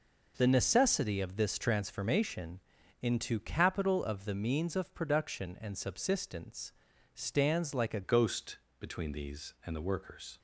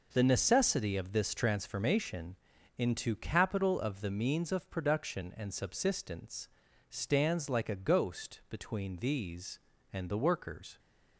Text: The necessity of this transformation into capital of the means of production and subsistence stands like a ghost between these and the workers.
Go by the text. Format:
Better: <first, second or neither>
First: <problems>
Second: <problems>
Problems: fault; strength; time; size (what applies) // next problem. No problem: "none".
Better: second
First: pauses between "transformation" and "into"; at 2.5 s; 0.42 s long // pauses between "subsistence" and "stands"; at 6.7 s; 0.40 s long // changes voice at "ghost"; from 8.0 s on; 2.3 s long // pauses between "ghost" and "between"; slight; at 8.5 s; 0.20 s long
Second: pauses between "transformation" and "into"; at 2.3 s; 0.42 s long // pauses between "subsistence" and "stands"; at 6.4 s; 0.39 s long